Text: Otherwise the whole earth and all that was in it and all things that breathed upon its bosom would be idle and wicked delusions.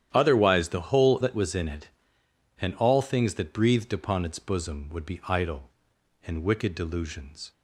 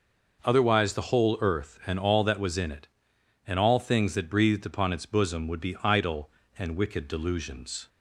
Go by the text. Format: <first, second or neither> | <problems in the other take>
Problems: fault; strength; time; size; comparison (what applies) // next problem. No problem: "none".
second | starts louder than the rest; strong; until 1.1 s; 10.5 dB // skips "earth and all"; at 1.1 s